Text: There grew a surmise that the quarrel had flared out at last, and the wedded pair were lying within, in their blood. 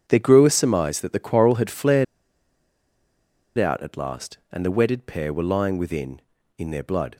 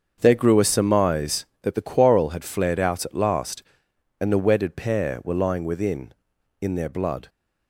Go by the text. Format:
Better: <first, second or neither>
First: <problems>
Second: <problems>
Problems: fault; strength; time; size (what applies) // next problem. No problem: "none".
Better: second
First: starts louder than the rest; strong; until 1.0 s; 7.5 dB // pauses between "flared" and "out"; strong; at 2.0 s; 1.5 s long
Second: starts louder than the rest; until 1.2 s; 7 dB